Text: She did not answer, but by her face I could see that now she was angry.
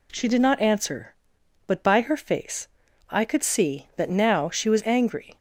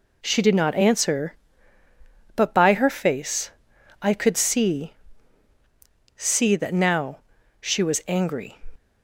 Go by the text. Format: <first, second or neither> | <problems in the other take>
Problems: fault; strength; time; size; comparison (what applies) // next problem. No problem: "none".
first | pauses between "face" and "I"; noticeable; at 3.4 s; 0.50 s long; also in the first // says "see" twice; at 6.1 s // pauses between "now" and "she"; at 7.1 s; 0.42 s long